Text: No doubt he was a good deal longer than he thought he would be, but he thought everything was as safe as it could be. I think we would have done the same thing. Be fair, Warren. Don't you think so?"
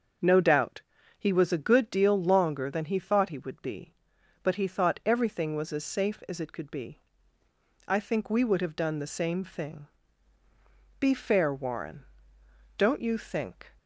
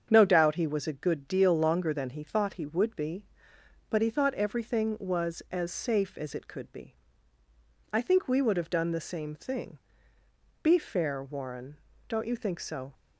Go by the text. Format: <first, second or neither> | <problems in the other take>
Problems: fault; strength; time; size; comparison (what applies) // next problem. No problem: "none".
second | starts louder than the rest; until 1.5 s; 6.5 dB; strong in the second // pauses between "doubt" and "he"; at 0.8 s; 0.38 s long // stops before "so"; at 13.7 s